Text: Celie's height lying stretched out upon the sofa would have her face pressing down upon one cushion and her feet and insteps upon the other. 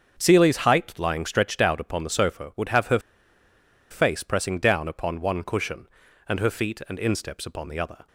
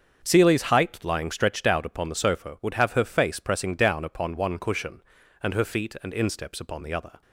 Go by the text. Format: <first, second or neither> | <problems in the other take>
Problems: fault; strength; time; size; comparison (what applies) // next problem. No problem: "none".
second | starts louder than the rest; until 1.2 s; 7 dB; also in the second // pauses between "her" and "face"; noticeable; at 2.9 s; 0.90 s long